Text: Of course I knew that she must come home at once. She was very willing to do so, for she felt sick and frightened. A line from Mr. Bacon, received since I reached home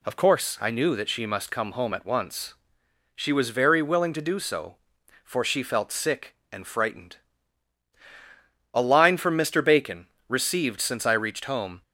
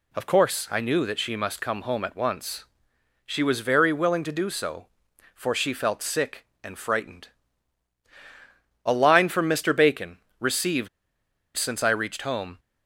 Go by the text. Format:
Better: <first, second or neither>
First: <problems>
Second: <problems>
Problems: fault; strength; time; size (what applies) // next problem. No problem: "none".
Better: first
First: none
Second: pauses between "received" and "since"; noticeable; at 10.8 s; 0.68 s long